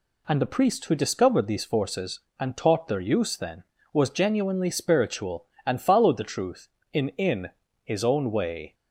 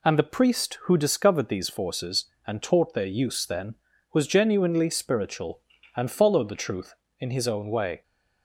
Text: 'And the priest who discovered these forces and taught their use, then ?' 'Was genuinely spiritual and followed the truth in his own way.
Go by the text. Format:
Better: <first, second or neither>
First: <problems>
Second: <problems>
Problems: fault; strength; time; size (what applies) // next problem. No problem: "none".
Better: second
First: says "in" twice; at 7.0 s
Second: none